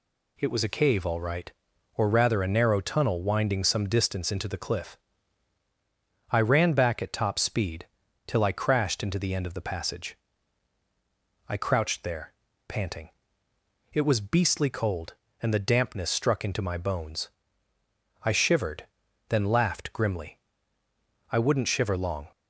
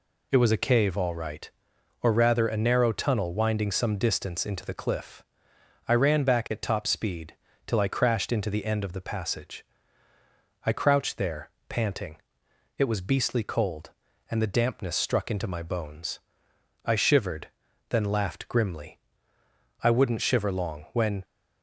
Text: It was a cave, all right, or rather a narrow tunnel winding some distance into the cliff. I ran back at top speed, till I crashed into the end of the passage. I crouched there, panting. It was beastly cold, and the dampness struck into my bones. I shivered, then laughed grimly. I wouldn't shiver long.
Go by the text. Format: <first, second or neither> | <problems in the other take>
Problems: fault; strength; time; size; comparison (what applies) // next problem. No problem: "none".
first | goes on to say "When"; slight; from 20.9 s on; 0.32 s long